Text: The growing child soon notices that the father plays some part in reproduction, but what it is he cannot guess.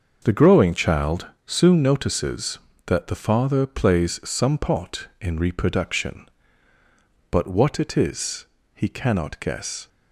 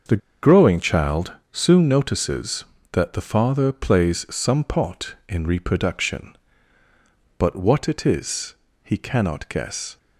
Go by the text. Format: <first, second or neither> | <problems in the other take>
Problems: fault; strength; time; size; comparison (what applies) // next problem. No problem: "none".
first | starts louder than the rest; until 1.3 s; 6 dB; also in the first // pauses between "The" and "growing"; slight; at 0.2 s; 0.24 s long // pauses between "child" and "soon"; slight; at 1.3 s; 0.18 s long; slight in the first // pauses between "is" and "he"; slight; at 8.5 s; 0.30 s long; slight in the first